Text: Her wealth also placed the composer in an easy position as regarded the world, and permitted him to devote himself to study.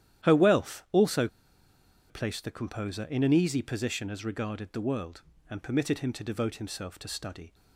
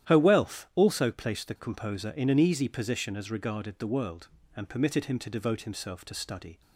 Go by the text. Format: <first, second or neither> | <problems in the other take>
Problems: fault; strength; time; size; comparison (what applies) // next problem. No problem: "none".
second | starts louder than the rest; strong; until 2.1 s; 11.5 dB; strong in the second // pauses between "also" and "placed"; noticeable; at 1.2 s; 0.82 s long